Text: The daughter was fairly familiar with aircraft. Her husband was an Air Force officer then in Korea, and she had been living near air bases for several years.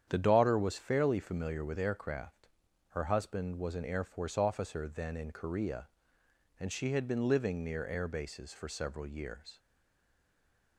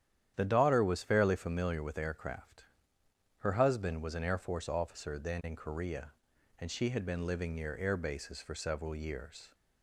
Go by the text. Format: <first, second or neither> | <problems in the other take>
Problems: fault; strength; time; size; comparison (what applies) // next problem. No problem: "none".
second | starts louder than the rest; strong; until 1.0 s; 9 dB; strong in the second // stays silent after the last word; noticeable; from 9.5 s on; 1.2 s long